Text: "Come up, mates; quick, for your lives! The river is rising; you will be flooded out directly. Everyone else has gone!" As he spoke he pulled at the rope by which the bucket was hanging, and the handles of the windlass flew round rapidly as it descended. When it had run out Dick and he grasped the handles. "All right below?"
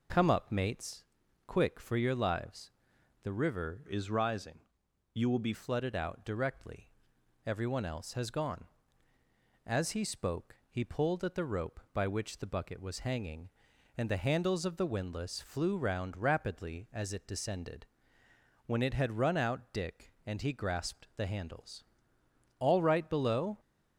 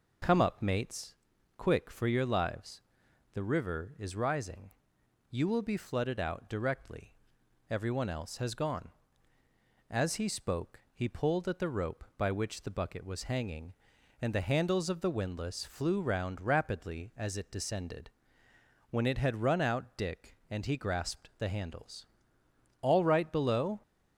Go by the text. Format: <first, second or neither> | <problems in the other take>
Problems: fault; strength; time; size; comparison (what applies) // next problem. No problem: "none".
second | changes voice from "is" to "be"; from 3.8 to 5.5 s; 1.7 s long // pauses between "spoke" and "he"; slight; at 10.5 s; 0.16 s long; slight in the second